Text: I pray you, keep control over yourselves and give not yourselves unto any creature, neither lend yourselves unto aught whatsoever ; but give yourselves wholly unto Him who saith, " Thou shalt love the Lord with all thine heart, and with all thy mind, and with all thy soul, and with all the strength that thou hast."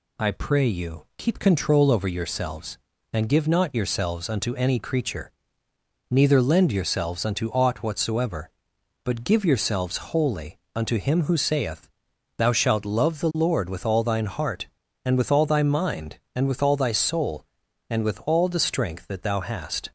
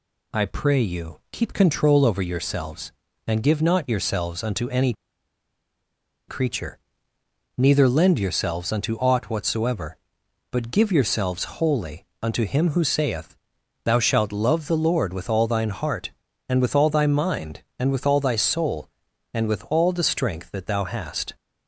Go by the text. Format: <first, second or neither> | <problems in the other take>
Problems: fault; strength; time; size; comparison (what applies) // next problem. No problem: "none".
first | pauses between "any" and "creature"; strong; at 4.9 s; 1.3 s long // pauses between "wholly" and "unto"; slight; at 12.0 s; 0.18 s long; slight in the first